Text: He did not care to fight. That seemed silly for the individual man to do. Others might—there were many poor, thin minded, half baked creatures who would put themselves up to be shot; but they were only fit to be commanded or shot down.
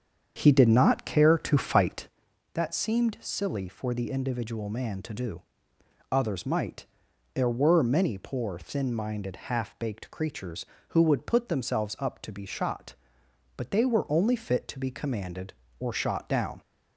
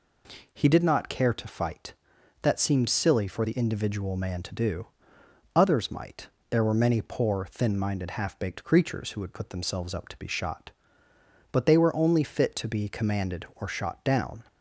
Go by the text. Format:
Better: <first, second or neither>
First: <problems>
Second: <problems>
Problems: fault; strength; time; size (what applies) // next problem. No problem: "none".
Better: second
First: starts louder than the rest; strong; until 2.2 s; 7.5 dB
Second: none